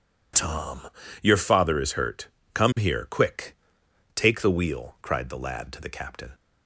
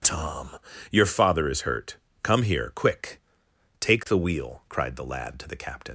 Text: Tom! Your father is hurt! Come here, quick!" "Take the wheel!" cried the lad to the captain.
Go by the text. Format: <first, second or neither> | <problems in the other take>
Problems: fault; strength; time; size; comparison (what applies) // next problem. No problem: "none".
first | leaves "captain" unfinished; at 5.8 s; 65 ms